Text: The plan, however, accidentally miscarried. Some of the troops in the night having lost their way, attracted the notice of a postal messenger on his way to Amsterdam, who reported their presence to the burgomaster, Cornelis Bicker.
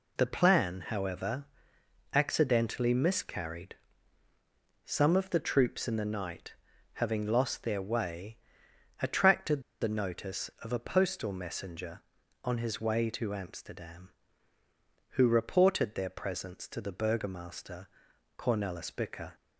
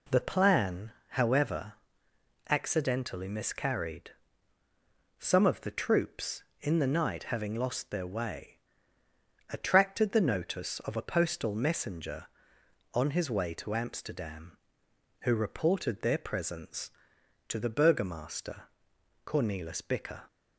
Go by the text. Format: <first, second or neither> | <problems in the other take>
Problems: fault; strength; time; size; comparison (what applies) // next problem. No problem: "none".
second | pauses between "night" and "having"; at 6.5 s; 0.40 s long // pauses between "attracted" and "the"; slight; at 9.6 s; 0.19 s long